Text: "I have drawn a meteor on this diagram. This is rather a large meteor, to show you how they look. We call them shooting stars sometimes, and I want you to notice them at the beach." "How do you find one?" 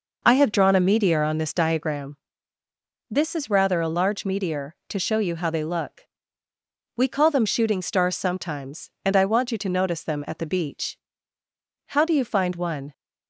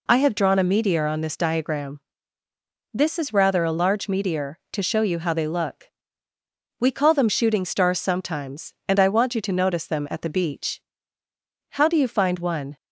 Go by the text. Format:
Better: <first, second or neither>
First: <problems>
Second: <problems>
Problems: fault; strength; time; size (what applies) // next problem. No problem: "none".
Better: second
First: starts louder than the rest; noticeable; until 2.1 s; 5 dB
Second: none